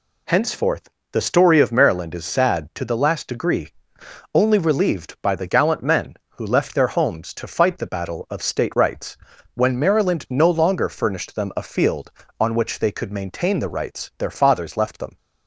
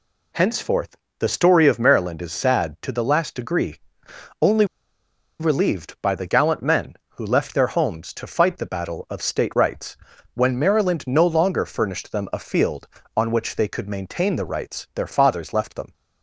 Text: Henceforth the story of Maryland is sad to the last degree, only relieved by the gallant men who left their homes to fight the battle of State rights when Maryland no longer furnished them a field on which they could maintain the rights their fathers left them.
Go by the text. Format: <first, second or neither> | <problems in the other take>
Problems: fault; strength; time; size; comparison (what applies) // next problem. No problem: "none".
first | pauses between "Henceforth" and "the"; slight; at 0.9 s; 0.22 s long; slight in the first // pauses between "only" and "relieved"; noticeable; at 4.6 s; 0.75 s long // pauses between "rights" and "when"; slight; at 9.9 s; 0.36 s long; slight in the first